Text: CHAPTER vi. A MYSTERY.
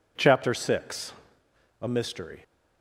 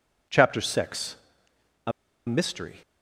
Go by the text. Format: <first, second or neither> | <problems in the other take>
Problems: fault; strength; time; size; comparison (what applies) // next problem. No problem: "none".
first | pauses between "A" and "MYSTERY"; slight; at 1.9 s; 0.35 s long